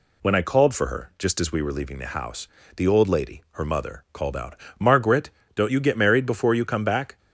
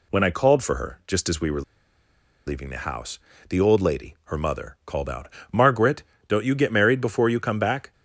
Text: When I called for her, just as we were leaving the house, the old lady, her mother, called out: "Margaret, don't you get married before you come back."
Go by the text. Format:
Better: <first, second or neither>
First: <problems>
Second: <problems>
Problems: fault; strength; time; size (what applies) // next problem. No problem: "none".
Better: first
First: none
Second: pauses between "were" and "leaving"; noticeable; at 1.6 s; 0.85 s long